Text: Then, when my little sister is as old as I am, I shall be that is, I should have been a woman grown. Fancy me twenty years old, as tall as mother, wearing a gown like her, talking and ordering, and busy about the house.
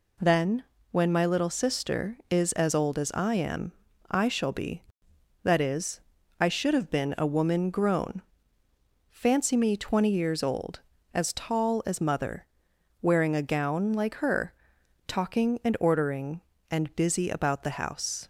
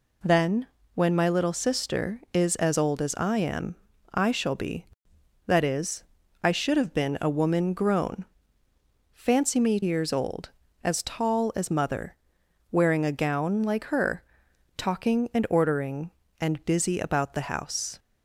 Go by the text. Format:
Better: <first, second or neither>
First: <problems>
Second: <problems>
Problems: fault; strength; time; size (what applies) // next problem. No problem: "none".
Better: first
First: none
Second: skips "twenty"; at 9.8 s